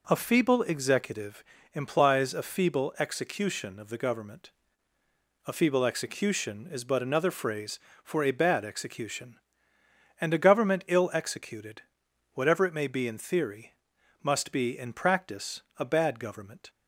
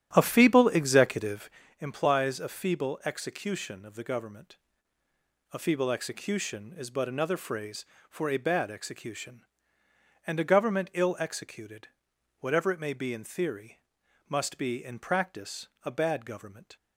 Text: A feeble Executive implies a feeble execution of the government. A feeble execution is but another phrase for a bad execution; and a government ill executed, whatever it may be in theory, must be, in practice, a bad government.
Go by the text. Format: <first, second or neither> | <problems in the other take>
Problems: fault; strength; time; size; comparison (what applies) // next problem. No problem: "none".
first | starts louder than the rest; strong; until 1.8 s; 11 dB // pauses between "Executive" and "implies"; slight; at 1.4 s; 0.32 s long; slight in the first